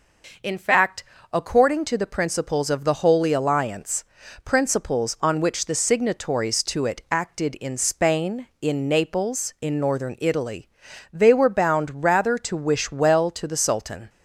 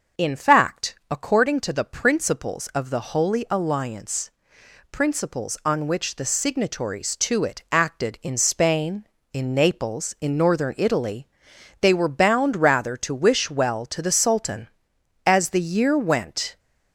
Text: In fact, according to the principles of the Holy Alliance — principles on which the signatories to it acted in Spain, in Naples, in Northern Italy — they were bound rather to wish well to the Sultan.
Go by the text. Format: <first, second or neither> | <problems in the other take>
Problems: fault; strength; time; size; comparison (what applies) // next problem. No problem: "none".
first | starts louder than the rest; noticeable; until 1.3 s; 6 dB // goes on to say "As the year went"; from 15.2 s on; 1.3 s long